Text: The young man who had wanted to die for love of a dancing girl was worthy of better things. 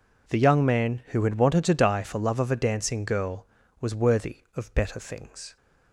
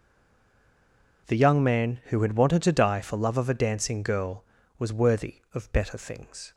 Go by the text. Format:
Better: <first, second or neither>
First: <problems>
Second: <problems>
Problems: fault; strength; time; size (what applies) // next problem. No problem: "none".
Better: first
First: none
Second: stays silent before the first word; noticeable; until 1.2 s; 1.2 s long